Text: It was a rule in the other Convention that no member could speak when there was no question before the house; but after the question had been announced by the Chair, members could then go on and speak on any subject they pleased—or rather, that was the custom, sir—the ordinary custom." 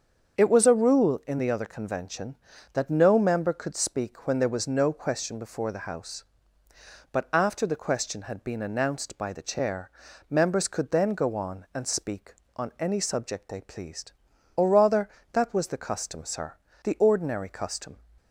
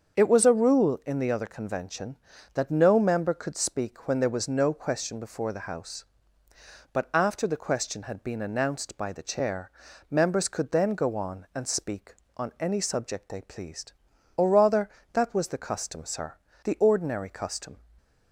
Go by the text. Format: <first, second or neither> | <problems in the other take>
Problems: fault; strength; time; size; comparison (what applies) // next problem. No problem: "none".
neither | starts louder than the rest; the same in both